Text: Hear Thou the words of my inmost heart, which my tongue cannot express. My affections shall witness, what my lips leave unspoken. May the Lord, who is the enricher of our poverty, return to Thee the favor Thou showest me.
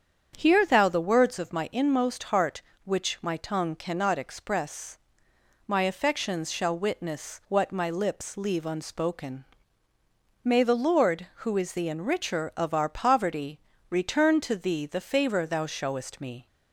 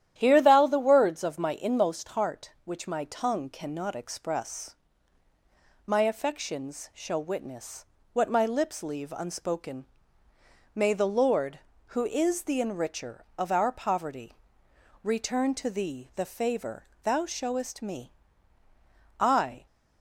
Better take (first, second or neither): first